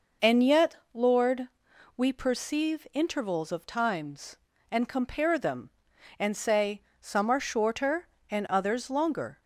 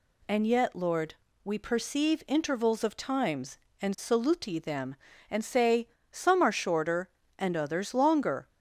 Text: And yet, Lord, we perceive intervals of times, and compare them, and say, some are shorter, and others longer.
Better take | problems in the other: first | says "saluti" for "compare"; at 3.9 s

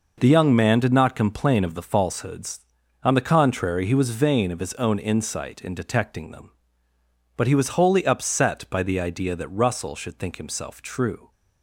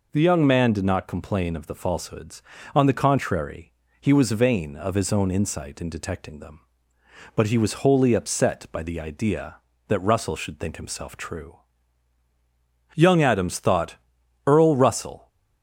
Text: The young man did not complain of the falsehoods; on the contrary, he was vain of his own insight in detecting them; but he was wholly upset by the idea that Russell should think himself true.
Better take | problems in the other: first | goes on to say "Young Adams thought Earl Russell"; strong; from 12.9 s on; 2.3 s long

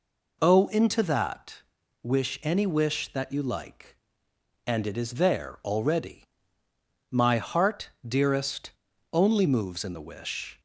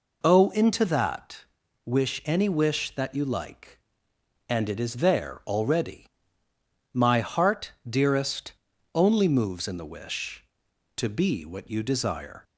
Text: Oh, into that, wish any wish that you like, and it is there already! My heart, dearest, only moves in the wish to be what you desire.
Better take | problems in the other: second | stops before "to be what you desire"; at 10.5 s

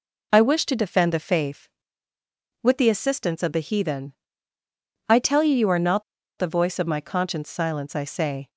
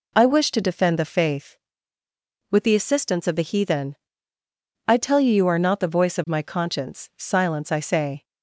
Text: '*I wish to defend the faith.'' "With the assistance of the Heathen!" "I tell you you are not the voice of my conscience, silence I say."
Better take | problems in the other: second | pauses between "not" and "the"; slight; at 6.0 s; 0.35 s long

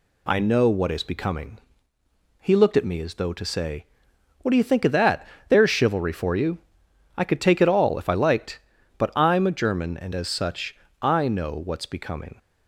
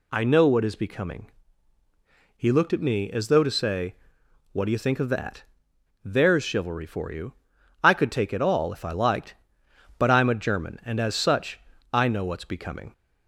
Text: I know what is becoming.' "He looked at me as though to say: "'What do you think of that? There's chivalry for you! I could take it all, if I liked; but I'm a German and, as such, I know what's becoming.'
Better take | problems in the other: neither | none

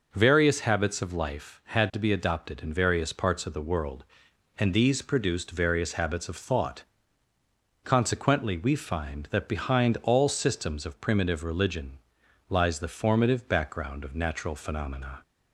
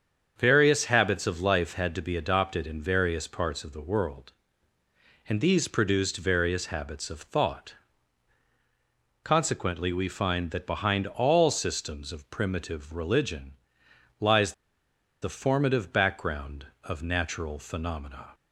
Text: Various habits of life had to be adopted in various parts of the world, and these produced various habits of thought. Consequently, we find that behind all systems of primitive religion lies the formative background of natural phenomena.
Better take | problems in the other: first | starts louder than the rest; strong; until 1.3 s; 7 dB // pauses between "religion" and "lies"; noticeable; at 13.5 s; 0.68 s long; noticeable in the first // pauses between "lies" and "the"; noticeable; at 14.5 s; 0.68 s long

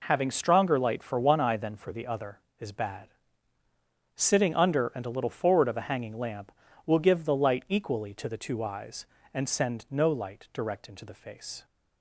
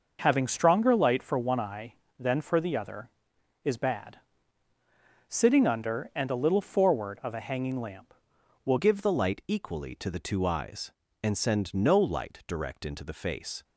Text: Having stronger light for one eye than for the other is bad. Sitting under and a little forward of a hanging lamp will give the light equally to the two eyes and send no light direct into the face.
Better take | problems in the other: first | changes voice at "give"; from 8.7 s on; 4.9 s long

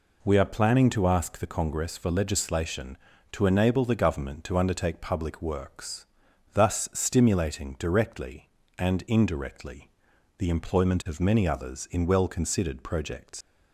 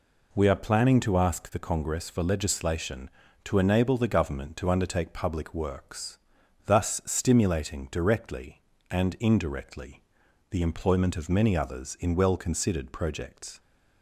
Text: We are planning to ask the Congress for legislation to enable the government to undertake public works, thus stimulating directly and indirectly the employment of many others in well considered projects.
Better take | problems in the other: second | pauses between "indirectly" and "the"; noticeable; at 9.8 s; 0.48 s long; noticeable in the second // leaves "projects" unfinished; at 13.4 s; 100 ms

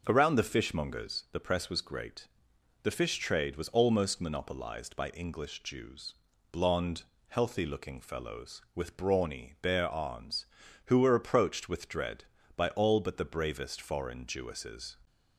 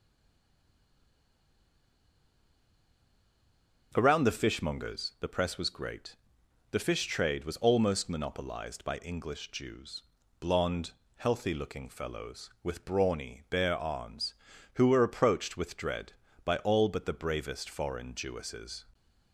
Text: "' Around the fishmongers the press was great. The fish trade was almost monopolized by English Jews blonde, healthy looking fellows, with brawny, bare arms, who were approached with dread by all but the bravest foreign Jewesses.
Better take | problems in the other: first | stays silent before the first word; strong; until 3.9 s; 3.9 s long // pauses between "Jews" and "blonde"; at 10.0 s; 0.40 s long; also in the first

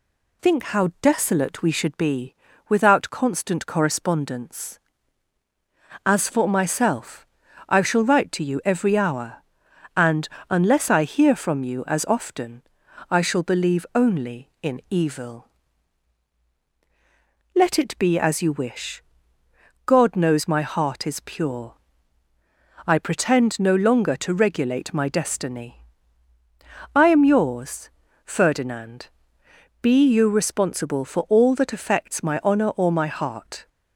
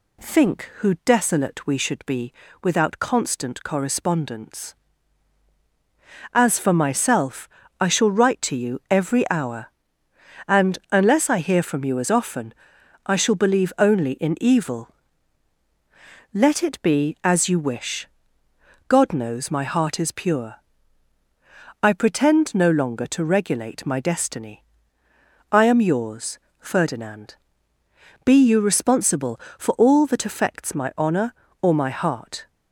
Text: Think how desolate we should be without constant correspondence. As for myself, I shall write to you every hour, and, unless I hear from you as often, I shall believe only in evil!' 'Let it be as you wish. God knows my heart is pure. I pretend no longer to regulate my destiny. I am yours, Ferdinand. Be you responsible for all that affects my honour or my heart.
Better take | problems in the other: first | says "who" for "how"; at 0.7 s // pauses between "be" and "without"; slight; at 2.3 s; 0.28 s long; slight in the first

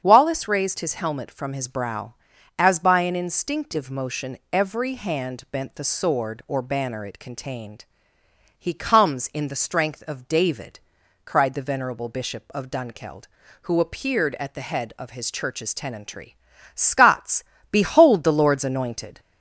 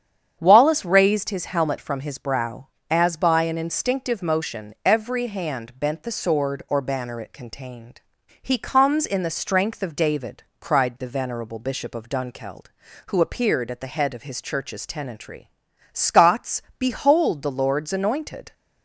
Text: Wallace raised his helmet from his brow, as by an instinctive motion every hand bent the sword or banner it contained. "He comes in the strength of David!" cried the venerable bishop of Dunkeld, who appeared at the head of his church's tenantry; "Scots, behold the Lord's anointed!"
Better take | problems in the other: neither | starts louder than the rest; strong; the same in both

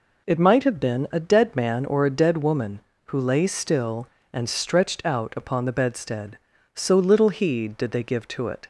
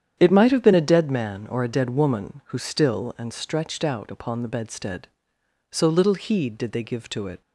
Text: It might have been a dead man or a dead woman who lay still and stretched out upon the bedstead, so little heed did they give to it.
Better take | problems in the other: first | starts louder than the rest; strong; until 1.2 s; 9 dB // skips "lay"; at 2.5 s

